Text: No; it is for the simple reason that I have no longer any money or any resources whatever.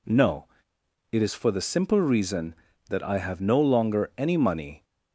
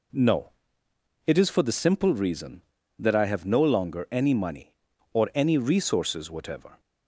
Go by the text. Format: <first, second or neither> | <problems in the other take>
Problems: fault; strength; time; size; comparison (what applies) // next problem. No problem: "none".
second | stops before "or any resources whatever"; at 4.8 s